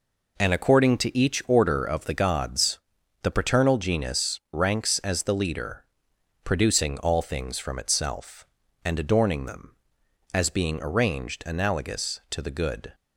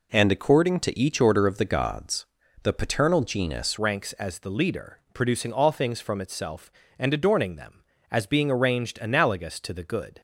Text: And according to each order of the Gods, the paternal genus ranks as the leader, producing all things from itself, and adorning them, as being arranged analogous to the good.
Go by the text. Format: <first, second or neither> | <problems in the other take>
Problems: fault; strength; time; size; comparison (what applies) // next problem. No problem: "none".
first | changes voice at "ranks"; from 3.7 s on; 6.5 s long